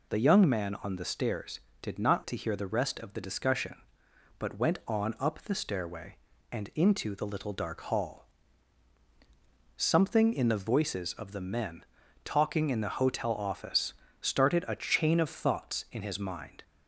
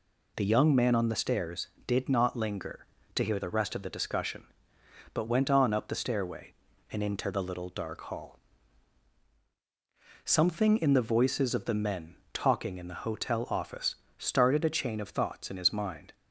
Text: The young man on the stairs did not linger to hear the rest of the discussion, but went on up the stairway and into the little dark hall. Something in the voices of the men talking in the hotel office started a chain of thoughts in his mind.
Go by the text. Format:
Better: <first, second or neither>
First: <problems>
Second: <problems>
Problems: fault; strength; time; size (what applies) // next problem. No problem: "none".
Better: second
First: skips "linger"; at 2.2 s // pauses between "men" and "talking"; at 11.8 s; 0.38 s long // pauses between "office" and "started"; slight; at 13.9 s; 0.28 s long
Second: pauses between "men" and "talking"; slight; at 12.1 s; 0.16 s long // pauses between "office" and "started"; slight; at 13.9 s; 0.22 s long